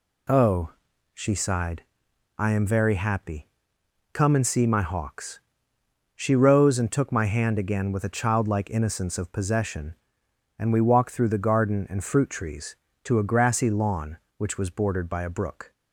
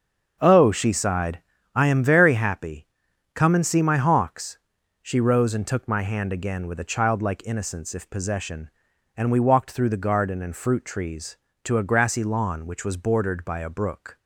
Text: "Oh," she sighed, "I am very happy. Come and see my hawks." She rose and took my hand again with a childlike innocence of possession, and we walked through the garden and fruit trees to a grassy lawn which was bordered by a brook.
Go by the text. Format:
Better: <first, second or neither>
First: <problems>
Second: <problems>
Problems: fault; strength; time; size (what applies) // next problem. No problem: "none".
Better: first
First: none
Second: starts louder than the rest; until 1.4 s; 7 dB // says "if" for "of"; at 7.9 s